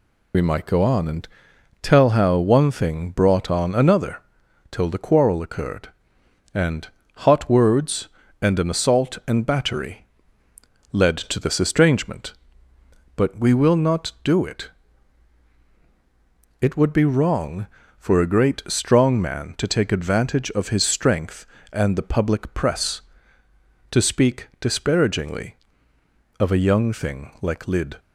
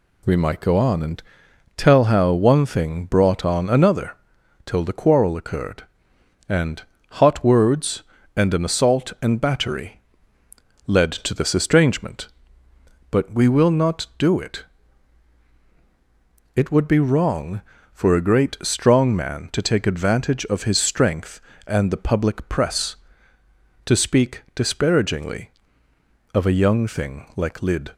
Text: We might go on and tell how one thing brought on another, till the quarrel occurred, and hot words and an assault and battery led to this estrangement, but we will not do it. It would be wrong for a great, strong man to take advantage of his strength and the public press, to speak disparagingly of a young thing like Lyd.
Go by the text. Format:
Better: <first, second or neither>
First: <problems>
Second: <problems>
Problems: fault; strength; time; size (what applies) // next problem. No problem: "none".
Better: second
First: loses the start of "We"; at 0.3 s; 65 ms // pauses between "and" and "tell"; noticeable; at 1.2 s; 0.54 s long // pauses between "and" and "hot"; slight; at 6.8 s; 0.28 s long // pauses between "battery" and "led"; noticeable; at 10.0 s; 0.86 s long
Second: pauses between "and" and "tell"; noticeable; at 1.2 s; 0.54 s long // pauses between "and" and "hot"; slight; at 6.8 s; 0.28 s long // pauses between "battery" and "led"; noticeable; at 9.9 s; 0.86 s long